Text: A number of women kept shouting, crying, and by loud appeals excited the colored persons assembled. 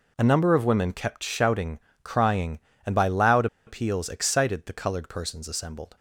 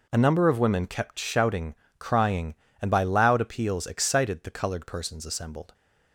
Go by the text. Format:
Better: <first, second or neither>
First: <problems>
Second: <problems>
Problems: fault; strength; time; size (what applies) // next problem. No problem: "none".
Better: second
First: pauses between "loud" and "appeals"; slight; at 3.4 s; 0.21 s long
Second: none